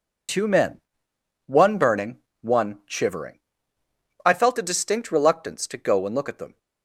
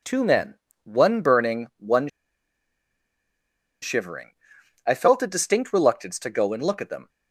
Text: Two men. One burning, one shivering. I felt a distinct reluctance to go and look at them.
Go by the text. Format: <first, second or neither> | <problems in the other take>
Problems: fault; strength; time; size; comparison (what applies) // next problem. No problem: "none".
first | pauses between "one" and "shivering"; strong; at 2.0 s; 1.7 s long